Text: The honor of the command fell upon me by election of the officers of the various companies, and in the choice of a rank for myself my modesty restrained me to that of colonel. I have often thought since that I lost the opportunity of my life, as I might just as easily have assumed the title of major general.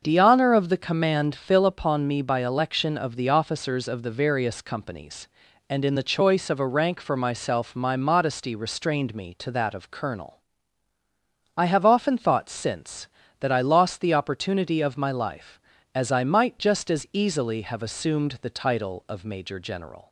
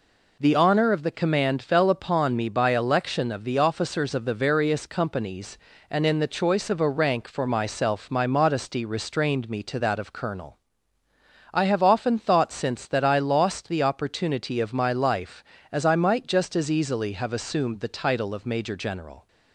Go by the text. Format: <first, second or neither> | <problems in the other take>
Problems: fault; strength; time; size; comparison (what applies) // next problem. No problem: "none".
second | starts louder than the rest; until 1.0 s; 6.5 dB // says "fill" for "fell"; at 1.3 s